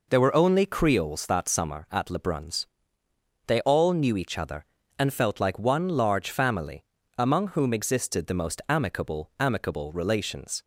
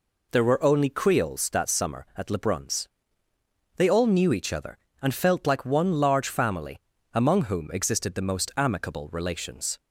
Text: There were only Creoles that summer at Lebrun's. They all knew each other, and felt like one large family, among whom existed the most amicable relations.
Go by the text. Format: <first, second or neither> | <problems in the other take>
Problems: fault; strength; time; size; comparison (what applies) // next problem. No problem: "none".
second | says "amicable" twice; at 9.3 s